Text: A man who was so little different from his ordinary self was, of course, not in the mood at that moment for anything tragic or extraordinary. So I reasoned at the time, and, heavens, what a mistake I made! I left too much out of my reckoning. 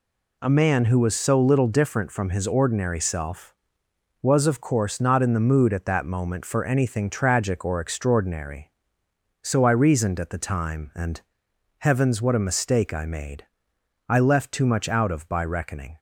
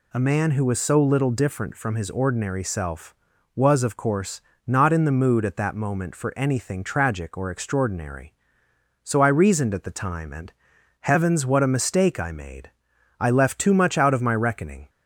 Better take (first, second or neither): second